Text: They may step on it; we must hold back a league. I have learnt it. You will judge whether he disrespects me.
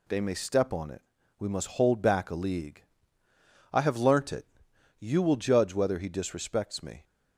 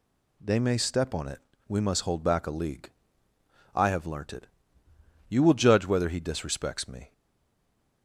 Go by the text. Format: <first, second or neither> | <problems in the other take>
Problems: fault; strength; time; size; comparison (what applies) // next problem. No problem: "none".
first | stays silent after the last word; slight; from 7.1 s on; 0.9 s long